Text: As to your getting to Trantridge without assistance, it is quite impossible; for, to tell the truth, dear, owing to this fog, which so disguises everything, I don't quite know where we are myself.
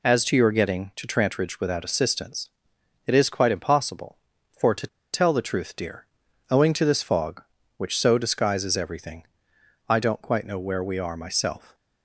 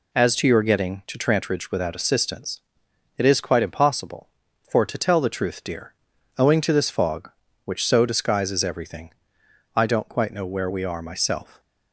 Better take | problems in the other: second | pauses between "to" and "tell"; slight; at 4.8 s; 0.25 s long

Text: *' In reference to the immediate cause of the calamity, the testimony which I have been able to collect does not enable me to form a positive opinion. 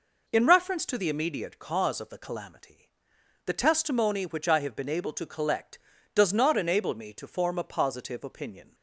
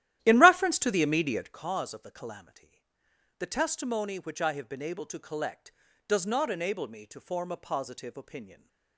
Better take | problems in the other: first | starts louder than the rest; strong; until 1.6 s; 13 dB

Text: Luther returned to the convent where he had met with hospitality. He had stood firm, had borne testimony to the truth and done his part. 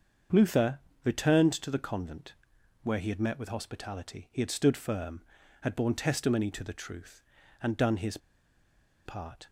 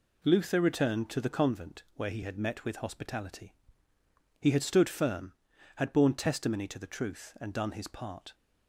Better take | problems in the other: second | starts louder than the rest; until 1.5 s; 7 dB // pauses between "Luther" and "returned"; slight; at 0.7 s; 0.24 s long // pauses between "convent" and "where"; noticeable; at 2.3 s; 0.50 s long // pauses between "his" and "part"; noticeable; at 8.1 s; 0.88 s long

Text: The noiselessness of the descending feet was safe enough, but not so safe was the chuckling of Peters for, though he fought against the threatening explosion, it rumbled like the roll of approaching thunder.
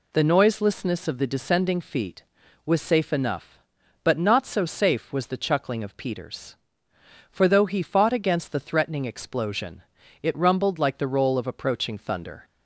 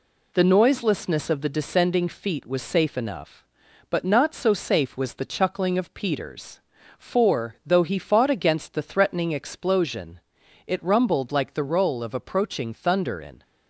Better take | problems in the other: first | goes on to say "In"; slight; from 13.2 s on; 0.22 s long

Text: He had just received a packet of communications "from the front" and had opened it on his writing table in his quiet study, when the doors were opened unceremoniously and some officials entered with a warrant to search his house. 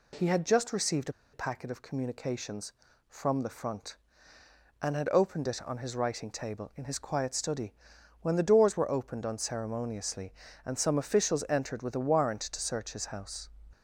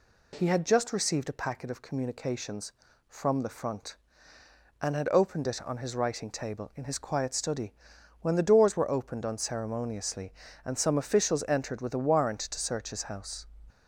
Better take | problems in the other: second | pauses between "received" and "a"; slight; at 1.0 s; 0.23 s long

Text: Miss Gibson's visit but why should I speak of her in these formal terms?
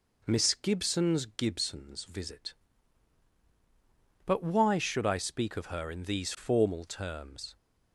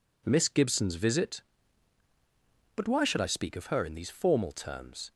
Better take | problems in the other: second | says "Gibson's" twice; at 1.2 s

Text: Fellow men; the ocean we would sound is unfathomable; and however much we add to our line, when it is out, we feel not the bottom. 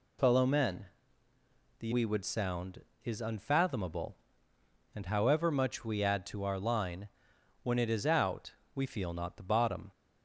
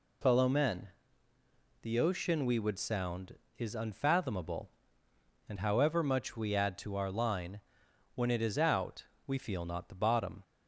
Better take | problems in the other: second | skips "ocean"; at 1.9 s

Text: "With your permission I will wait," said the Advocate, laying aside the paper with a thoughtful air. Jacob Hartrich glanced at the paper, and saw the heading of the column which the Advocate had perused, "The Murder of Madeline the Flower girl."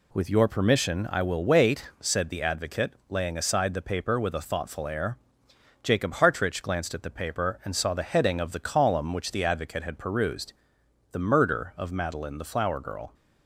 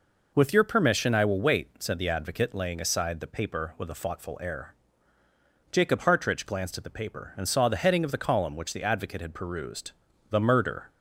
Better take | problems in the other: first | stops before "of Madeline the Flower girl"; at 10.8 s

